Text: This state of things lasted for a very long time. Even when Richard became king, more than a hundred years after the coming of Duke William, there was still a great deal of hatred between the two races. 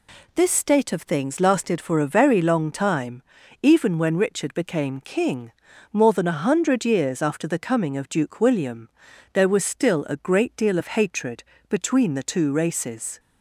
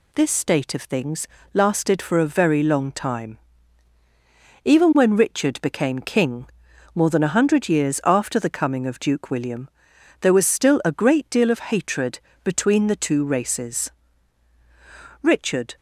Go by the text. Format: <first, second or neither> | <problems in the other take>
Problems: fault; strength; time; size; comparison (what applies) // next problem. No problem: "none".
first | pauses between "things" and "lasted"; slight; at 1.2 s; 0.26 s long // pauses between "hatred" and "between"; slight; at 12.1 s; 0.24 s long; slight in the first // goes on to say "Richard"; from 15.2 s on; 0.54 s long